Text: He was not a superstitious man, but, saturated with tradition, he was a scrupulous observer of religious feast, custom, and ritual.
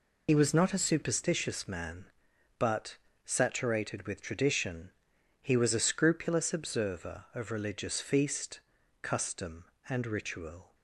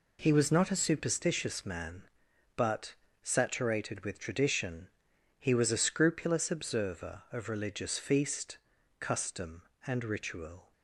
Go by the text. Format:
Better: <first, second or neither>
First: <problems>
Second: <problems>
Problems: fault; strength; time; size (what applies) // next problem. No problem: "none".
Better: second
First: loses the start of "He"; at 0.2 s; 75 ms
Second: none